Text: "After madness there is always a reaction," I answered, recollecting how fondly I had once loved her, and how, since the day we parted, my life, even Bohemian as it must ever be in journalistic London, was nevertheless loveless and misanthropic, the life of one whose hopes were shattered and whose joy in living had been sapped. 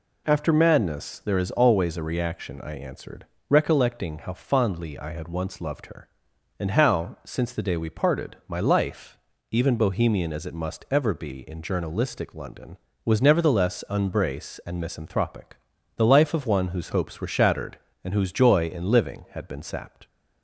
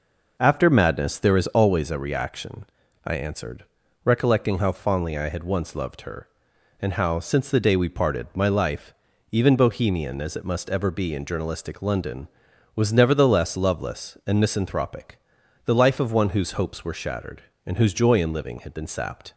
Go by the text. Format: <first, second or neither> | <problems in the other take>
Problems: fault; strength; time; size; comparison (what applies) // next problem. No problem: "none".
second | says "unbrace" for "loveless"; at 13.9 s